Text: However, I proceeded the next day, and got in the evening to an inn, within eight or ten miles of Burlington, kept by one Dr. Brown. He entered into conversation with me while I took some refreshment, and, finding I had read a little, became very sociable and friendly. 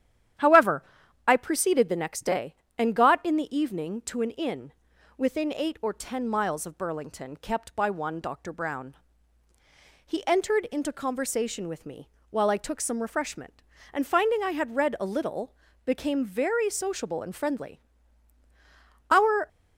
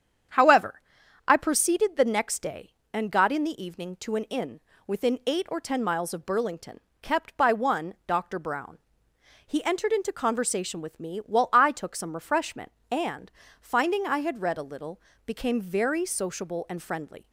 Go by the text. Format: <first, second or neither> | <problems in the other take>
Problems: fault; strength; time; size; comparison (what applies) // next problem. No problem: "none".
second | starts louder than the rest; strong; until 1.8 s; 10.5 dB; strong in the second // pauses between "me" and "while"; slight; at 12.0 s; 0.22 s long // goes on to say "Our"; slight; from 19.0 s on; 0.38 s long